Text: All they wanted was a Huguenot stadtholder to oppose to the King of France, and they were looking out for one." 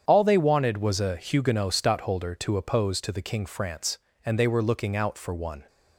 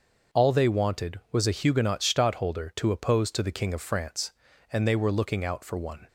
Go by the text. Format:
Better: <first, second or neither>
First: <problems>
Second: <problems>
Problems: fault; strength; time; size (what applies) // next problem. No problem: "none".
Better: second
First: starts louder than the rest; strong; until 1.0 s; 8 dB // skips "of"; at 3.4 s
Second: starts louder than the rest; noticeable; until 1.4 s; 6 dB